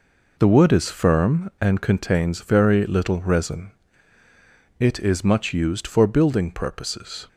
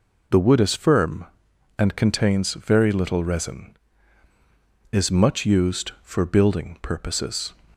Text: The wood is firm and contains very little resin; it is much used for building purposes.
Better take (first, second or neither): first